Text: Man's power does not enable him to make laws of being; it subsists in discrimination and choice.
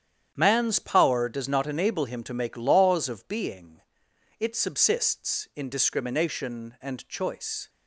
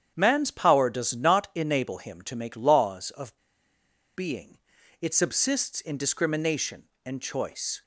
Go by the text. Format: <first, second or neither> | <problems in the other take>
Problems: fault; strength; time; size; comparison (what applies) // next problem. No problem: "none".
first | starts louder than the rest; strong; until 1.1 s; 9 dB; strong in the first // pauses between "of" and "being"; noticeable; at 3.3 s; 0.81 s long